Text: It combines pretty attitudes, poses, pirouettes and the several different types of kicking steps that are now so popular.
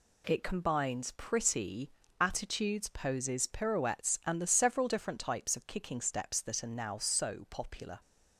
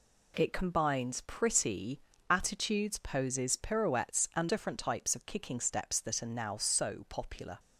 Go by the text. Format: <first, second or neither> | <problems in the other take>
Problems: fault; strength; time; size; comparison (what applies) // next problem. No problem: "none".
first | pauses between "pretty" and "attitudes"; slight; at 2.0 s; 0.28 s long; slight in the first // skips "the several"; at 4.4 s